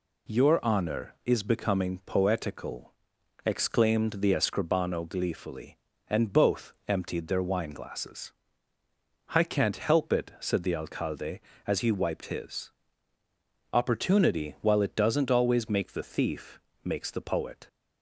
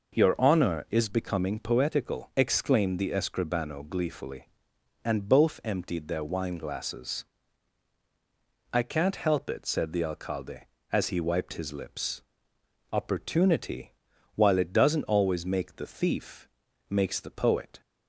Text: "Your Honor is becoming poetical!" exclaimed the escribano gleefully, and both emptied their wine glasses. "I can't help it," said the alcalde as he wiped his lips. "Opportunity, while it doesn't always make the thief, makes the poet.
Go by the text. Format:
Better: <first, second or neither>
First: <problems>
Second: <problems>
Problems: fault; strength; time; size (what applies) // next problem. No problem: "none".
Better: second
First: skips "lips"; at 13.2 s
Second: none